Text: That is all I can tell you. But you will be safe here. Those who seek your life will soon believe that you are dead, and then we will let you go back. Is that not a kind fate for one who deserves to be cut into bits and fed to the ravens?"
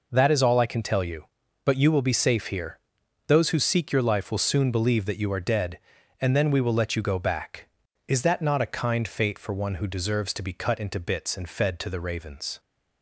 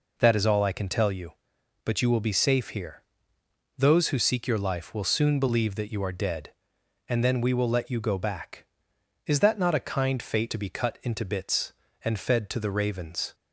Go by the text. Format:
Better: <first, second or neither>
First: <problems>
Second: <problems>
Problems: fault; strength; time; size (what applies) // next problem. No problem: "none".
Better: first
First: none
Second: skips "for one who deserves"; at 10.5 s